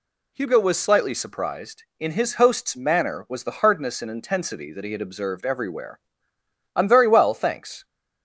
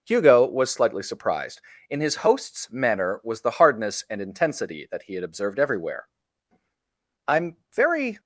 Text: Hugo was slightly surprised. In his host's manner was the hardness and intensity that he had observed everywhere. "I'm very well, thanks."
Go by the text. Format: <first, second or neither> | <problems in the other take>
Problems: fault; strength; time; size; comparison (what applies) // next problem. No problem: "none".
first | pauses between "I'm" and "very"; slight; at 7.5 s; 0.18 s long // stops before "well thanks"; at 8.1 s